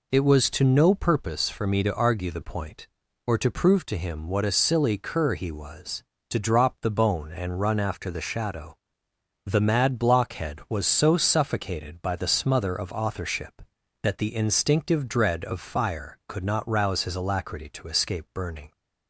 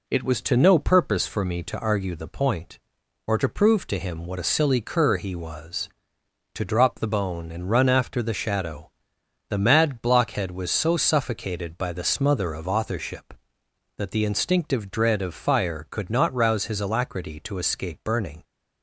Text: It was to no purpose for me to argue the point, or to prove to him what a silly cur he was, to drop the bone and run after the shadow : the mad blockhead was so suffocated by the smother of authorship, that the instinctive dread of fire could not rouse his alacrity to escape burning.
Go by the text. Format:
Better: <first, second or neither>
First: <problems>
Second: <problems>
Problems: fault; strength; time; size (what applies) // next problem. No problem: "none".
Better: neither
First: none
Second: none